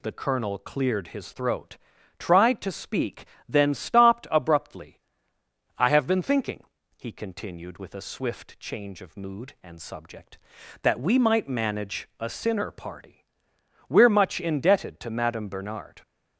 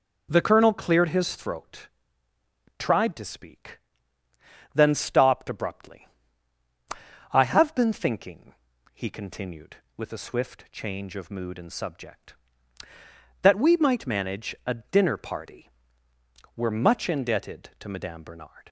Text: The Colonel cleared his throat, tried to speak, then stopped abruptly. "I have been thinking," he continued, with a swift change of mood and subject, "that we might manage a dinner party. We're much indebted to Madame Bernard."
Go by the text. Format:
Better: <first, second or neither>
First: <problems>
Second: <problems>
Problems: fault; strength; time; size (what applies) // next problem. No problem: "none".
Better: second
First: says "sinner" for "dinner"; at 12.2 s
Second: none